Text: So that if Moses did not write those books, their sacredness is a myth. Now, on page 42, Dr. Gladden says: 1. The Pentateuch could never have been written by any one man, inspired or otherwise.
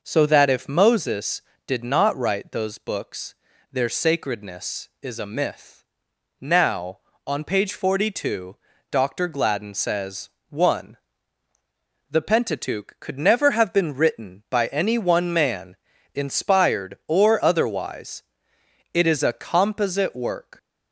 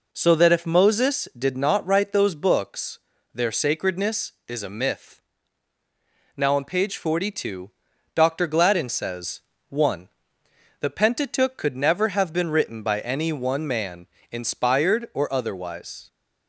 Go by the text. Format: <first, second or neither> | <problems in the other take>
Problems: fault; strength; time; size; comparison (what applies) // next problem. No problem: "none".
second | goes on to say "It is a composite work"; from 18.9 s on; 1.6 s long